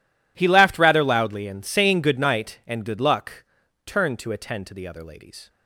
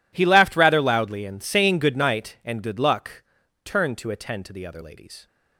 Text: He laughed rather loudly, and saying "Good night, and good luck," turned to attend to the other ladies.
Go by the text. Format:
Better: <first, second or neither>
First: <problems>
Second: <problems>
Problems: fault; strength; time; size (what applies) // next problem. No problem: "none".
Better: neither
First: none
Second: none